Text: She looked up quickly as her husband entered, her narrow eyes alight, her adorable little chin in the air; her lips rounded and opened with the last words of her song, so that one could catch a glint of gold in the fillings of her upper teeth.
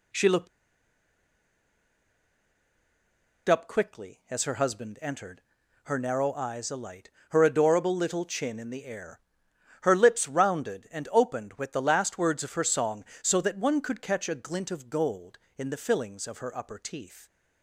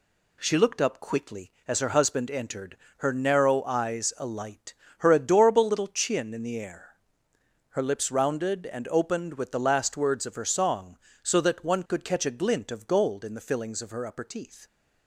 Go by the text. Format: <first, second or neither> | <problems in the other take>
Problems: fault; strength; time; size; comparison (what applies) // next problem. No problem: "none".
second | pauses between "looked" and "up"; strong; at 0.4 s; 3.0 s long